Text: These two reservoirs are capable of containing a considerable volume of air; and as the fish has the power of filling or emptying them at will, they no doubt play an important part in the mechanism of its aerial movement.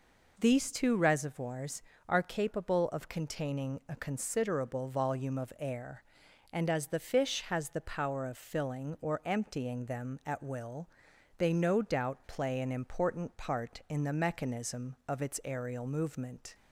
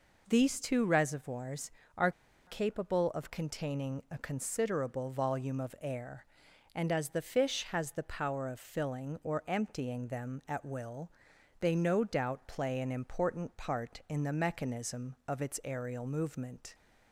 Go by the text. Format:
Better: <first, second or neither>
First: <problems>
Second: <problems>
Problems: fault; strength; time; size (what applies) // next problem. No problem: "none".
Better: first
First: none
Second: pauses between "are" and "capable"; slight; at 2.1 s; 0.35 s long